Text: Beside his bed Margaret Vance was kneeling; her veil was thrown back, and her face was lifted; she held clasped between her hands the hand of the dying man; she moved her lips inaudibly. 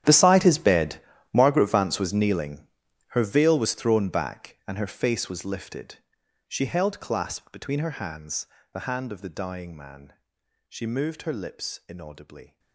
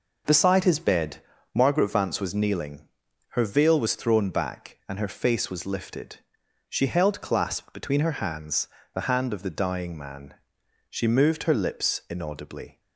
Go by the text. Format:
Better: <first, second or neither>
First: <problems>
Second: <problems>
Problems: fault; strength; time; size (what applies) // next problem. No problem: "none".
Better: second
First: gets quieter; strong; throughout; 18.5 dB // pauses between "bed" and "Margaret"; slight; at 0.9 s; 0.36 s long // pauses between "hands" and "the"; slight; at 8.4 s; 0.26 s long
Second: pauses between "bed" and "Margaret"; slight; at 1.1 s; 0.36 s long // pauses between "hands" and "the"; slight; at 8.6 s; 0.26 s long